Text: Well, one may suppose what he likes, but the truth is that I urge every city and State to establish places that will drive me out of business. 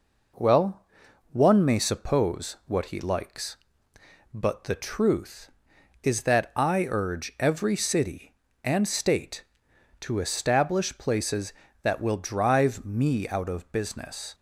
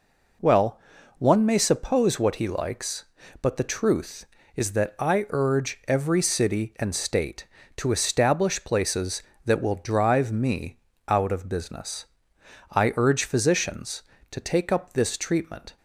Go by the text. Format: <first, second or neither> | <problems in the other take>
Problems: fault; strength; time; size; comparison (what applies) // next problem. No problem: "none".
first | pauses between "me" and "out"; slight; at 10.7 s; 0.30 s long // goes on to say "I urge physicians to take up this treatment"; strong; from 12.7 s on; 3.0 s long